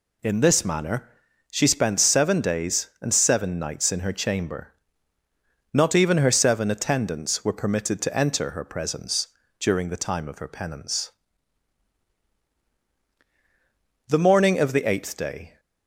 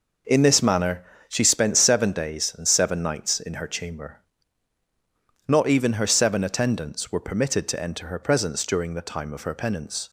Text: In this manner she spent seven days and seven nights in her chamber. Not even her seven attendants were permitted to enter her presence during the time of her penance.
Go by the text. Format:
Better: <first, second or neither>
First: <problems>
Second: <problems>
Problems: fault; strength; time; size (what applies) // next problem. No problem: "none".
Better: second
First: pauses between "manner" and "she"; at 1.0 s; 0.42 s long // pauses between "presence" and "during"; slight; at 9.2 s; 0.32 s long // goes on to say "The morning of the eighth day"; from 14.0 s on; 1.5 s long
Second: pauses between "manner" and "she"; slight; at 1.0 s; 0.24 s long